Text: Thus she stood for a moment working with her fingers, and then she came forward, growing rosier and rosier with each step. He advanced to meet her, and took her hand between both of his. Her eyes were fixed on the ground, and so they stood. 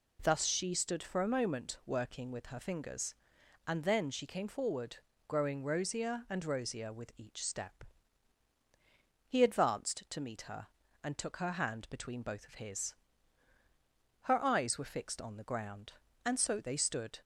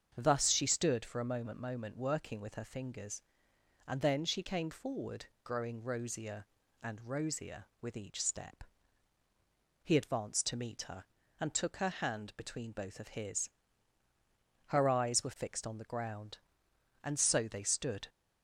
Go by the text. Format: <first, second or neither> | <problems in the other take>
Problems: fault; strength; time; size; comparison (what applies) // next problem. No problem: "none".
first | starts louder than the rest; strong; until 1.1 s; 7 dB // says "moment" twice; at 1.5 s